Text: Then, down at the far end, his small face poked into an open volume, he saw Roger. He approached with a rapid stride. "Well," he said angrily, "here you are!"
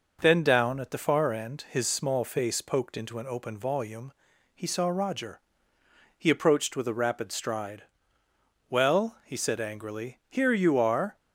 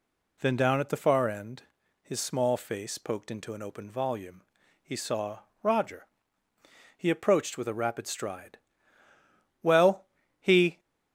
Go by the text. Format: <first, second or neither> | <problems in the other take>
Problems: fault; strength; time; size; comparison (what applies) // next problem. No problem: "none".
first | pauses between "saw" and "Roger"; slight; at 5.3 s; 0.22 s long // stops before "said angrily here you are"; at 10.7 s